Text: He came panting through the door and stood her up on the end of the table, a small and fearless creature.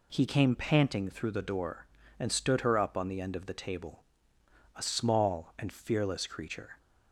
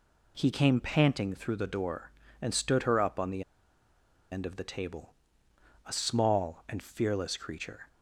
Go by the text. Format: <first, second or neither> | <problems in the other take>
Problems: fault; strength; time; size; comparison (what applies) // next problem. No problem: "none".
first | pauses between "the" and "end"; noticeable; at 3.4 s; 0.89 s long